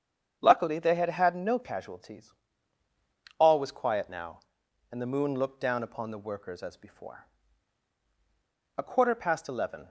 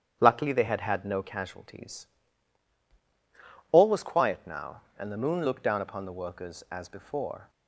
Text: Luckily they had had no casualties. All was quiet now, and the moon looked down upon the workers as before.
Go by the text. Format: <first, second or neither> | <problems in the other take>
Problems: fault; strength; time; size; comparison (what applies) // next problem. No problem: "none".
second | starts louder than the rest; strong; until 1.4 s; 8 dB; strong in the second // goes on to say "A quarter past eleven"; noticeable; from 8.7 s on; 1.1 s long